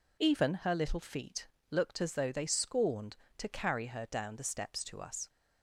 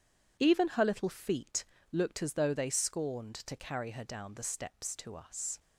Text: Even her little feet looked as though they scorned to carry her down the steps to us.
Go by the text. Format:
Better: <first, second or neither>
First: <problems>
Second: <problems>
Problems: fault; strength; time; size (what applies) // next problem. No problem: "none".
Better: neither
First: pauses between "feet" and "looked"; slight; at 1.4 s; 0.22 s long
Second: pauses between "feet" and "looked"; slight; at 1.6 s; 0.30 s long